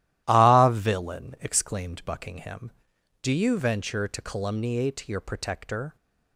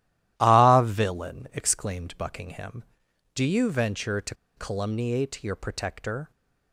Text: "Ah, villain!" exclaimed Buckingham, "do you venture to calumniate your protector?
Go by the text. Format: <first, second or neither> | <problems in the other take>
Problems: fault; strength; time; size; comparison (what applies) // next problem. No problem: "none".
first | starts louder than the rest; strong; until 1.3 s; 13.5 dB; strong in the first // pauses between "to" and "calumniate"; slight; at 4.3 s; 0.22 s long